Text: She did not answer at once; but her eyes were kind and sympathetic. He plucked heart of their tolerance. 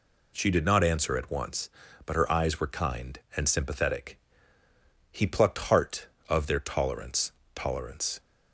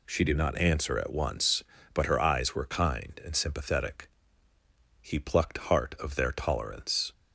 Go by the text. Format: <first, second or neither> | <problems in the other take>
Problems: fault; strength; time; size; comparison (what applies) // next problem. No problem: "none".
second | says "tolerance" twice; at 7.5 s